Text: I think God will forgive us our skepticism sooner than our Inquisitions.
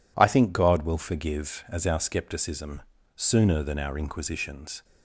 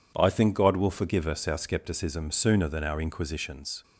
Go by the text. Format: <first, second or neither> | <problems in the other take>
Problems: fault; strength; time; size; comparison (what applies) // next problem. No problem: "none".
second | says "as" for "us"; at 1.6 s // pauses between "skepticism" and "sooner"; slight; at 2.8 s; 0.34 s long